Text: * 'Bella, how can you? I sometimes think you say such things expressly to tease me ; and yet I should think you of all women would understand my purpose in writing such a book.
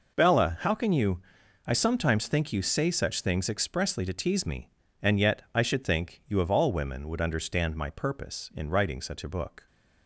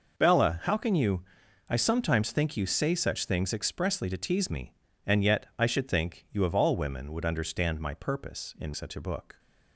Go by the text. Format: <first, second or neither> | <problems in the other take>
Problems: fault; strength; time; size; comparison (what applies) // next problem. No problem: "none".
first | skips "writing"; at 8.7 s